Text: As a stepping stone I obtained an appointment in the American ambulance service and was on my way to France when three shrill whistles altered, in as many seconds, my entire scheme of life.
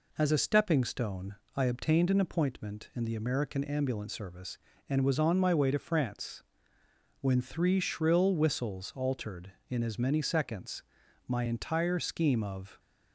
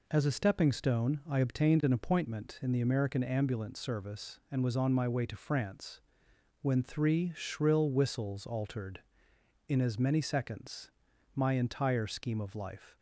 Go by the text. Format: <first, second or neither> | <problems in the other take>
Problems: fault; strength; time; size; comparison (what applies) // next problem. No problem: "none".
second | pauses between "stone" and "I"; slight; at 1.3 s; 0.20 s long // pauses between "France" and "when"; noticeable; at 6.4 s; 0.80 s long; noticeable in the second // stops before "life"; at 12.7 s